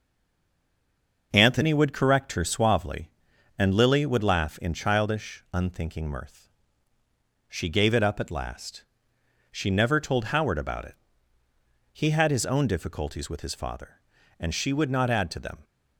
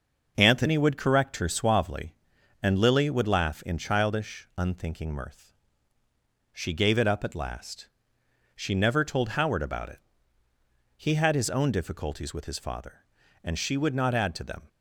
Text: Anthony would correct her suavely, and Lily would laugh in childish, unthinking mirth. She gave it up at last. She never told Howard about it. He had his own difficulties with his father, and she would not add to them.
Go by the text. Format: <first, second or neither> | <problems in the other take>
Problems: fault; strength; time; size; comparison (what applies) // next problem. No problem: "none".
second | stays silent before the first word; noticeable; until 1.3 s; 1.3 s long // starts louder than the rest; noticeable; until 2.3 s; 6 dB; noticeable in the second